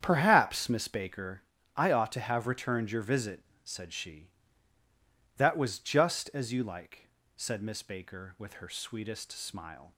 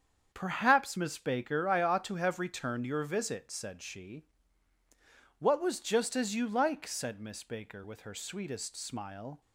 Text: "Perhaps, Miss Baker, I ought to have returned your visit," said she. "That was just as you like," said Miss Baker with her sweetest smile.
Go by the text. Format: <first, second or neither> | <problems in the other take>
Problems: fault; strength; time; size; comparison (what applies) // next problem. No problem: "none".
first | starts louder than the rest; strong; until 1.3 s; 7.5 dB; strong in the first // says "What" for "That"; at 5.4 s